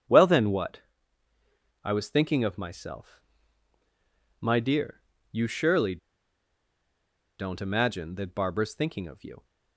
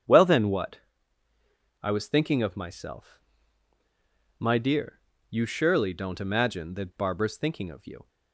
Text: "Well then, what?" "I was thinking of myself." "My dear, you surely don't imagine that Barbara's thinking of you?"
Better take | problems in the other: second | starts louder than the rest; strong; until 2.0 s; 7.5 dB; strong in the second // pauses between "surely" and "don't"; strong; at 5.9 s; 1.4 s long

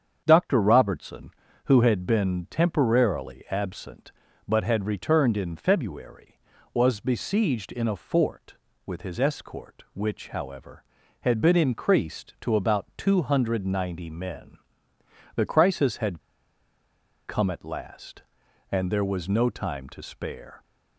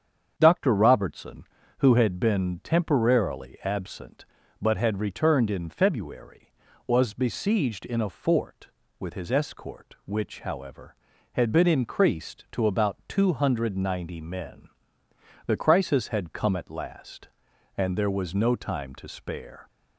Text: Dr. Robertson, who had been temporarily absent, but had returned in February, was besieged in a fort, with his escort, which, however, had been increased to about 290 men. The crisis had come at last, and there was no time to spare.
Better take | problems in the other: second | starts louder than the rest; strong; until 1.2 s; 7.5 dB; strong in the second // pauses between "had" and "come"; at 16.2 s; 1.0 s long

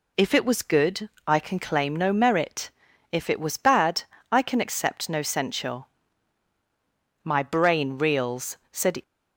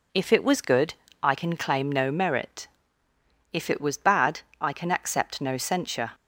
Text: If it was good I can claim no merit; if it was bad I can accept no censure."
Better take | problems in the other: second | pauses between "good" and "I"; slight; at 1.0 s; 0.18 s long; slight in the second // pauses between "bad" and "I"; slight; at 4.0 s; 0.28 s long; slight in the second // goes on to say "My brain reels said"; strong; from 7.2 s on; 1.7 s long

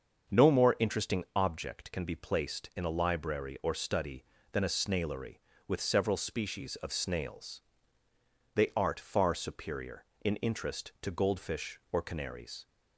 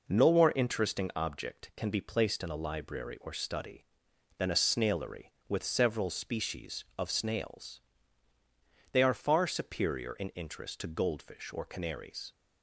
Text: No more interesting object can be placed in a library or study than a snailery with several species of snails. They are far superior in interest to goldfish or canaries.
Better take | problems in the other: second | starts louder than the rest; until 1.4 s; 6.5 dB // says "art" for "are"; at 8.7 s

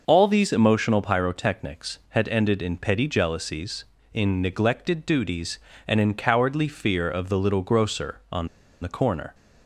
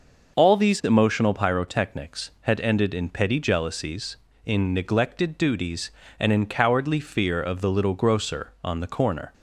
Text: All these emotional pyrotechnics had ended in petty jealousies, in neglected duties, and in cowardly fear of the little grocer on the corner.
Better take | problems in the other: second | pauses between "on" and "the"; slight; at 8.4 s; 0.34 s long

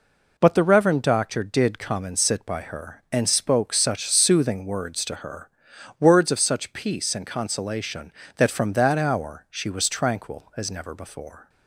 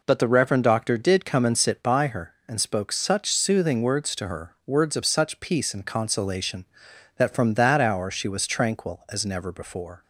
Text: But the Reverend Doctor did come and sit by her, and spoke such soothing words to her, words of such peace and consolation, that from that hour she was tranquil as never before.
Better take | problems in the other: neither | none

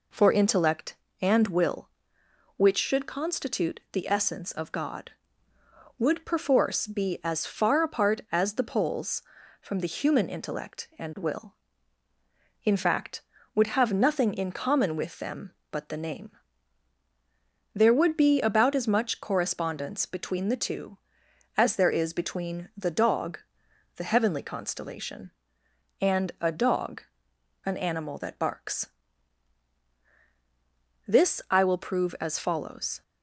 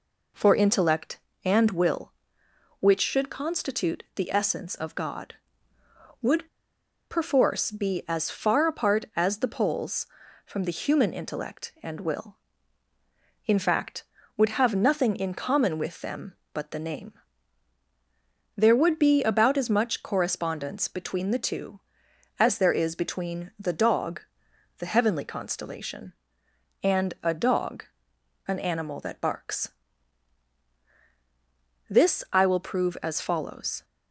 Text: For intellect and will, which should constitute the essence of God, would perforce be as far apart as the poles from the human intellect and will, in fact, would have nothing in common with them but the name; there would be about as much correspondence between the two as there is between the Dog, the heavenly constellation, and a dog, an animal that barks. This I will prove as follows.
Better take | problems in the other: first | pauses between "would" and "perforce"; noticeable; at 6.4 s; 0.61 s long

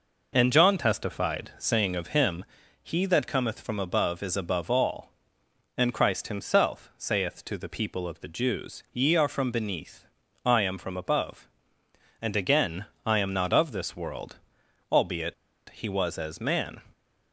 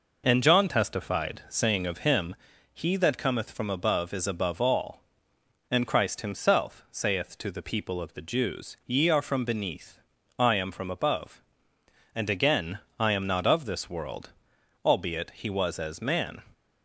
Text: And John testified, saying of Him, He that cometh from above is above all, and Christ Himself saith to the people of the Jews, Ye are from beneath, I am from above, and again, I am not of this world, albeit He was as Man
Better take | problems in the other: second | pauses between "albeit" and "He"; slight; at 15.3 s; 0.34 s long

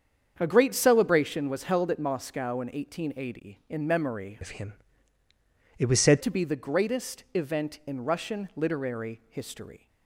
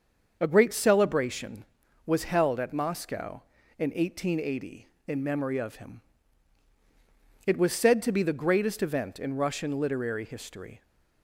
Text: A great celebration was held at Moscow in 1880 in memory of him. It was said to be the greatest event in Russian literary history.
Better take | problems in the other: second | starts louder than the rest; strong; until 1.3 s; 7.5 dB; also in the second // changes voice from "of" to "said"; from 4.4 to 6.2 s; 1.8 s long

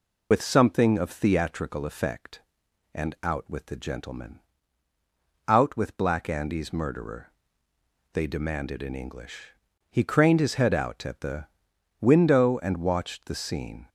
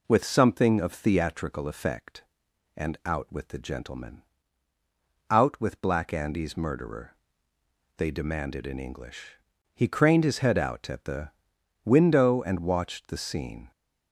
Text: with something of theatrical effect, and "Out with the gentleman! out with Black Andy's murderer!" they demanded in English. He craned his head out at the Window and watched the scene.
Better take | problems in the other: second | loses the start of "with"; at 0.3 s; 65 ms // pauses between "the" and "Window"; noticeable; at 11.4 s; 0.54 s long; noticeable in the second

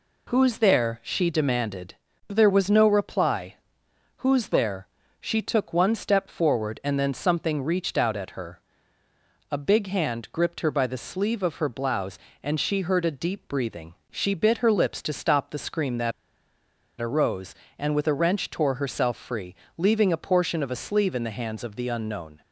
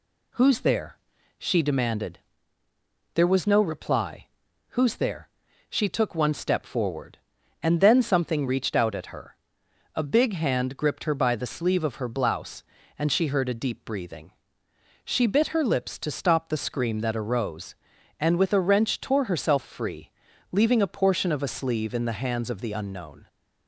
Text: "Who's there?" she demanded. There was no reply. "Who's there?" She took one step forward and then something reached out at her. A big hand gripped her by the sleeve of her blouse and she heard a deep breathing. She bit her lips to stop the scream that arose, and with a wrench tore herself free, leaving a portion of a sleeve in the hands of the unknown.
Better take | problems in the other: second | pauses between "that" and "arose"; noticeable; at 16.1 s; 0.89 s long

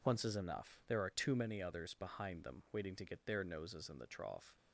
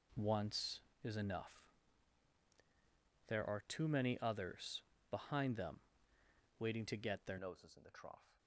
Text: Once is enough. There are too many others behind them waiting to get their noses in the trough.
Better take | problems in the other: first | pauses between "others" and "behind"; slight; at 4.8 s; 0.26 s long // pauses between "them" and "waiting"; noticeable; at 5.7 s; 0.80 s long // changes voice at "noses"; from 7.3 s on; 1.0 s long

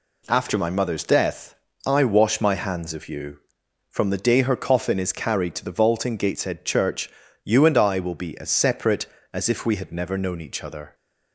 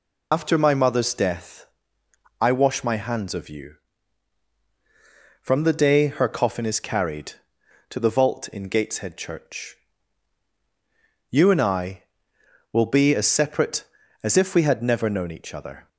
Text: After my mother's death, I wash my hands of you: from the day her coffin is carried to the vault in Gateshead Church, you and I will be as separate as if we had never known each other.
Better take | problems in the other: first | loses the start of "After"; at 0.3 s; 65 ms

